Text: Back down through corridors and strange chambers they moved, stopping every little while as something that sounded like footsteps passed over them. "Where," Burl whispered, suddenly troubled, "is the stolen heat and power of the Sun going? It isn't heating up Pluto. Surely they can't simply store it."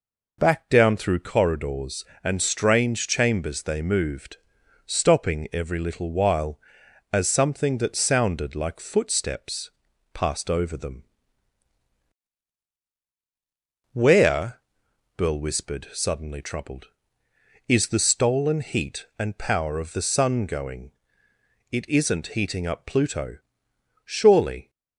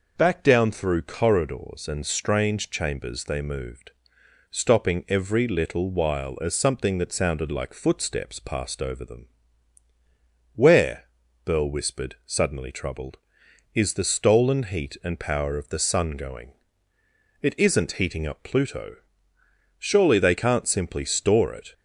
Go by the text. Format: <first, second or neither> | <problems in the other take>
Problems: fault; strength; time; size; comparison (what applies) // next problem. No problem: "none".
second | pauses between "footsteps" and "passed"; at 9.6 s; 0.44 s long // stops before "they can't simply store it"; at 24.6 s